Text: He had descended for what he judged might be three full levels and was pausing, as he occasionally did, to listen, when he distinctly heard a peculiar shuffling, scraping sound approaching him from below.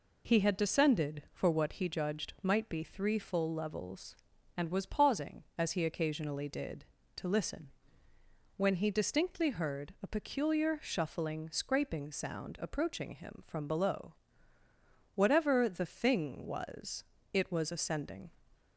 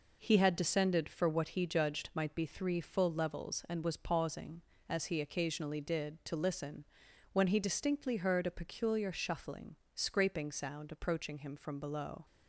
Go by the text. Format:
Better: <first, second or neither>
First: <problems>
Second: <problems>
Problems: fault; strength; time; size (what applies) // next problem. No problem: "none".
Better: second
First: goes on to say "Whatever the thing was it was ascending"; strong; from 15.1 s on; 3.1 s long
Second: none